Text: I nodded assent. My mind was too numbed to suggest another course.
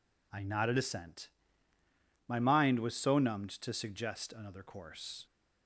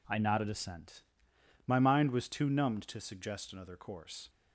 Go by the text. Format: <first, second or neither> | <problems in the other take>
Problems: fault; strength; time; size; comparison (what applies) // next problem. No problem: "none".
second | says "so" for "too"; at 2.9 s